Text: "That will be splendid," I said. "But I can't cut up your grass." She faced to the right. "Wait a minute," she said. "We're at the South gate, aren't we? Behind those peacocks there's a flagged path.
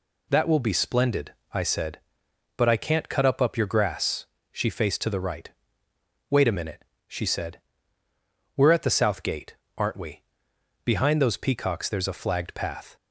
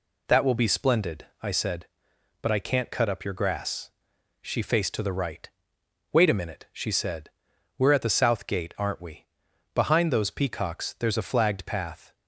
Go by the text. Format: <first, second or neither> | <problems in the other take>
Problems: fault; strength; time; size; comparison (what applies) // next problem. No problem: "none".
second | says "up" twice; at 3.3 s